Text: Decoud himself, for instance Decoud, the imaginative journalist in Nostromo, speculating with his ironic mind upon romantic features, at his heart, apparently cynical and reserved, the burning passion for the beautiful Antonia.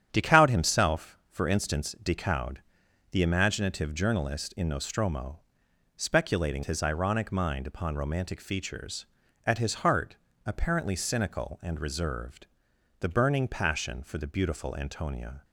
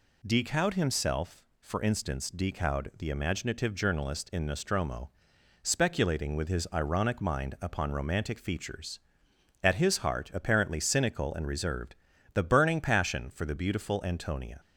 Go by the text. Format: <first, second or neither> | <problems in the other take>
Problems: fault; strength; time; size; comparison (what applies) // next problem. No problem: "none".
second | starts louder than the rest; strong; until 1.1 s; 9.5 dB // skips "with"; at 6.6 s